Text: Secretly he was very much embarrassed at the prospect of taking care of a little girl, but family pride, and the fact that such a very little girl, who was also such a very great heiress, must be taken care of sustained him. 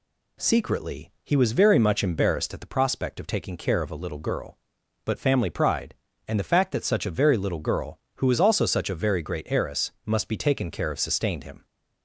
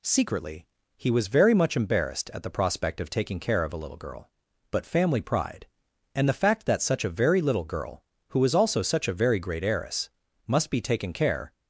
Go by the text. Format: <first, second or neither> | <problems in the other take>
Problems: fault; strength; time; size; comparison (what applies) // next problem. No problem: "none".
first | pauses between "Secretly" and "he"; slight; at 0.6 s; 0.30 s long // stops before "of sustained him"; at 11.5 s